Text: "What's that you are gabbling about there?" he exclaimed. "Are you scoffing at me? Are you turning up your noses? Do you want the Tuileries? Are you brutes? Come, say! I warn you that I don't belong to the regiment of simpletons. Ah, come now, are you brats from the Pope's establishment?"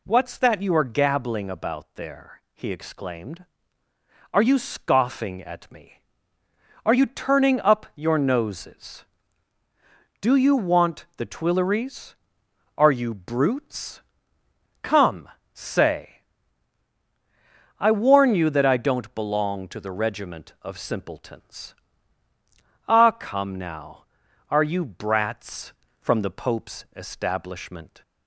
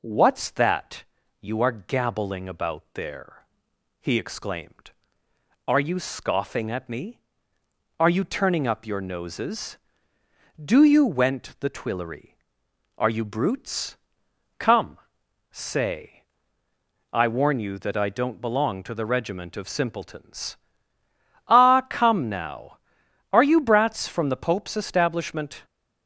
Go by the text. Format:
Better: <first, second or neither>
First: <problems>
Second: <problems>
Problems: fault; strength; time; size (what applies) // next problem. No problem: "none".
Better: first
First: none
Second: pauses between "that" and "you"; at 1.0 s; 0.38 s long // says "went" for "want"; at 11.0 s